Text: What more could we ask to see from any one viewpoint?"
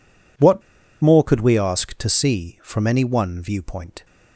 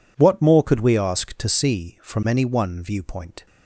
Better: second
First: pauses between "What" and "more"; at 0.6 s; 0.39 s long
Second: none

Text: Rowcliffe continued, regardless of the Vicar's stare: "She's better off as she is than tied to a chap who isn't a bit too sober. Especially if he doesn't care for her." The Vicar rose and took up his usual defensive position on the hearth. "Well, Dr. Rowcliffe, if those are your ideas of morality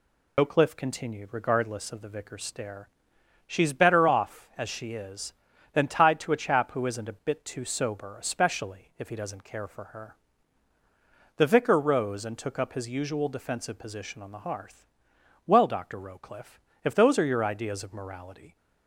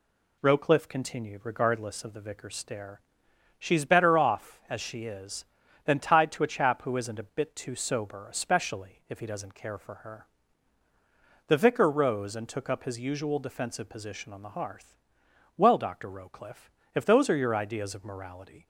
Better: second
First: loses the start of "Rowcliffe"; at 0.3 s; 100 ms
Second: none

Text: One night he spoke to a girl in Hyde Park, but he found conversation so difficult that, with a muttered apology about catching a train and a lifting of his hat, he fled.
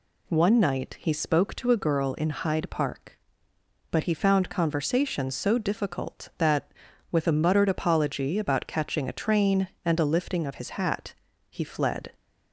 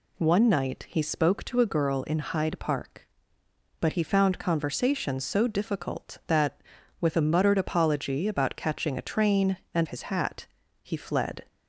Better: first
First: none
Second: skips "a lifting of"; at 9.8 s

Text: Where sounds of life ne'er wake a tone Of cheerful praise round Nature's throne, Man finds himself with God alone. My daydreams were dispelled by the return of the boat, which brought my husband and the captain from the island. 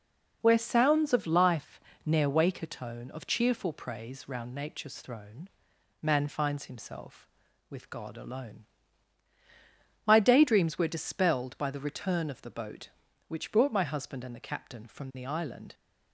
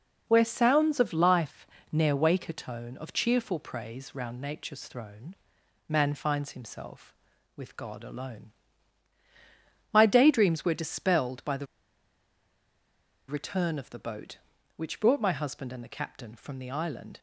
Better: first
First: pauses between "life" and "ne'er"; slight; at 1.8 s; 0.24 s long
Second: pauses between "life" and "ne'er"; slight; at 1.6 s; 0.24 s long // pauses between "the" and "return"; strong; at 11.6 s; 1.6 s long

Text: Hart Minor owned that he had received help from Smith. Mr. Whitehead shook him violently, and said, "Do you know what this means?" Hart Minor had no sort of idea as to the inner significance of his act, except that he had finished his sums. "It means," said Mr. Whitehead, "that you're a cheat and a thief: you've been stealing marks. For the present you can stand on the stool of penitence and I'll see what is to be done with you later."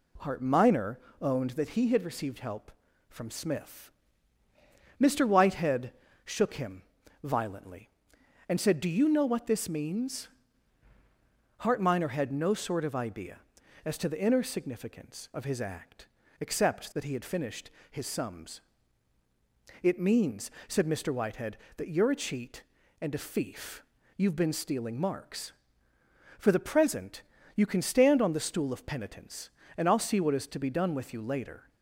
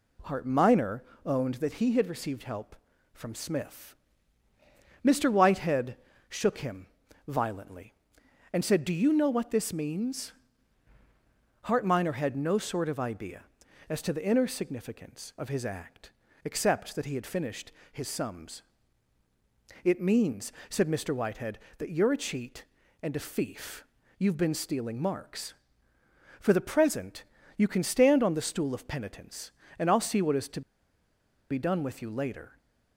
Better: first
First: pauses between "Minor" and "owned"; slight; at 0.9 s; 0.22 s long // pauses between "Whitehead" and "shook"; slight; at 5.9 s; 0.32 s long // pauses between "him" and "violently"; at 6.8 s; 0.40 s long // pauses between "finished" and "his"; slight; at 17.6 s; 0.22 s long // pauses between "present" and "you"; slight; at 27.2 s; 0.32 s long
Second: pauses between "Minor" and "owned"; slight; at 1.0 s; 0.22 s long // pauses between "Whitehead" and "shook"; slight; at 5.9 s; 0.32 s long // pauses between "him" and "violently"; at 6.8 s; 0.40 s long // pauses between "finished" and "his"; slight; at 17.7 s; 0.22 s long // pauses between "present" and "you"; slight; at 27.2 s; 0.32 s long // pauses between "to" and "be"; noticeable; at 30.6 s; 0.90 s long

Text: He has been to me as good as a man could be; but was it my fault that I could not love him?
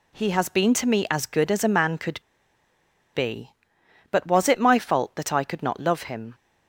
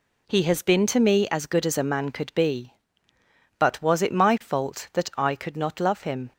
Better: second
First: pauses between "could" and "be"; noticeable; at 2.1 s; 0.94 s long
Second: none

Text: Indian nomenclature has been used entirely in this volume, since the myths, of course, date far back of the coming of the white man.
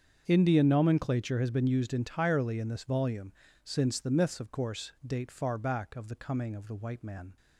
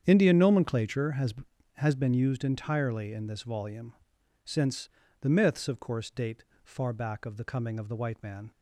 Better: first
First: starts louder than the rest; strong; until 1.2 s; 7 dB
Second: starts louder than the rest; strong; until 1.0 s; 8 dB // says "has" twice; at 1.7 s // pauses between "since" and "the"; slight; at 4.8 s; 0.34 s long // pauses between "date" and "far"; slight; at 6.4 s; 0.20 s long

